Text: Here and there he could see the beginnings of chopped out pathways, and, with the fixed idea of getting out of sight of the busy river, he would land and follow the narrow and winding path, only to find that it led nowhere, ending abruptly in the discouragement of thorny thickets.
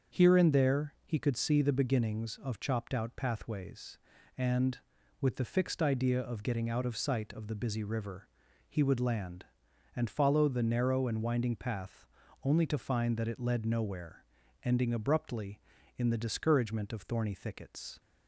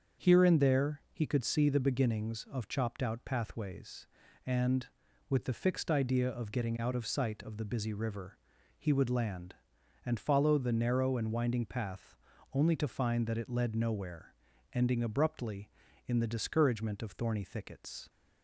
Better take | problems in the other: neither | starts louder than the rest; the same in both

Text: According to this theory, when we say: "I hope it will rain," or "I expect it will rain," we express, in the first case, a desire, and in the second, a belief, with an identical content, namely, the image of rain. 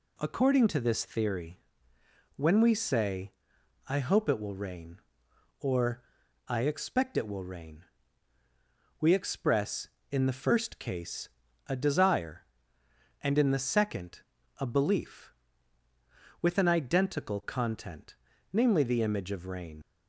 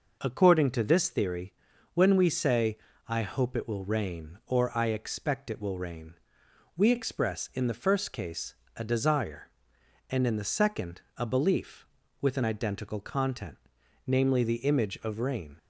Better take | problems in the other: second | pauses between "or" and "I"; noticeable; at 6.0 s; 0.46 s long // leaves "rain" unfinished; at 19.8 s; 90 ms

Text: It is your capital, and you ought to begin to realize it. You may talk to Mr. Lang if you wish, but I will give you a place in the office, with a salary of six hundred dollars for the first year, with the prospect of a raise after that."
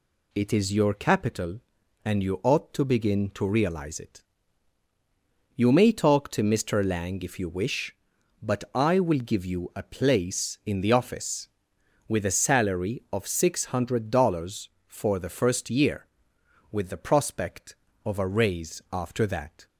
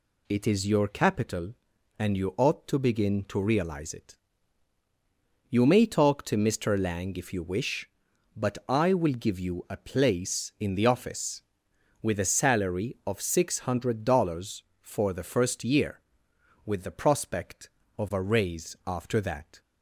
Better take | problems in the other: neither | none

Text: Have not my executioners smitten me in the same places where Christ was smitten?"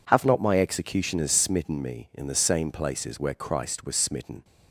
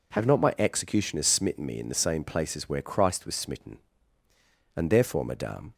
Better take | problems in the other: first | goes on to say "And therefore madame"; noticeable; from 4.7 s on; 0.98 s long

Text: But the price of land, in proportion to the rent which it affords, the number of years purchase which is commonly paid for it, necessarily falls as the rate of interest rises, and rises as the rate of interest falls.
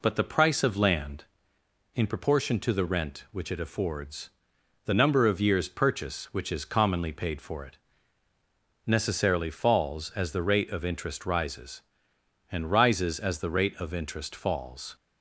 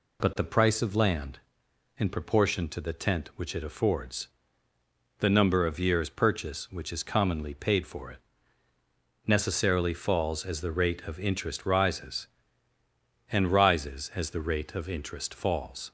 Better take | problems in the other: first | says "tent" for "rent"; at 2.9 s

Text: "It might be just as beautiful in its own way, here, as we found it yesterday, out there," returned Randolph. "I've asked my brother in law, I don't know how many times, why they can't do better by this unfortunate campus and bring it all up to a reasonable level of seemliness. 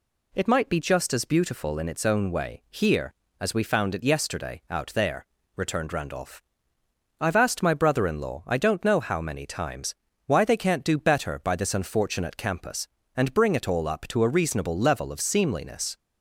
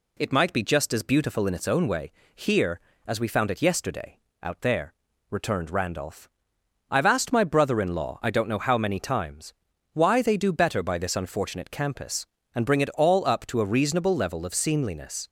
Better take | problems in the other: first | skips "can't"; at 10.3 s

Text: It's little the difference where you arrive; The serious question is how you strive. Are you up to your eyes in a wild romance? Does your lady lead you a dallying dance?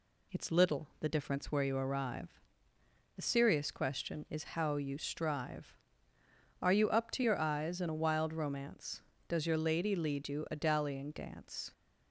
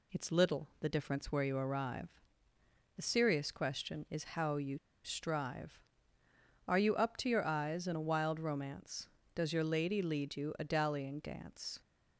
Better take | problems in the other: first | pauses between "you" and "strive"; slight; at 4.7 s; 0.26 s long

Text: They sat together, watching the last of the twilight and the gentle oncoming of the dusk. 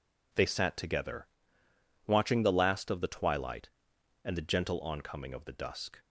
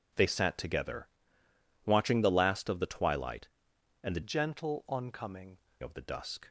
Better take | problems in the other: first | changes voice from "gentle" to "oncoming"; from 4.2 to 5.5 s; 1.3 s long

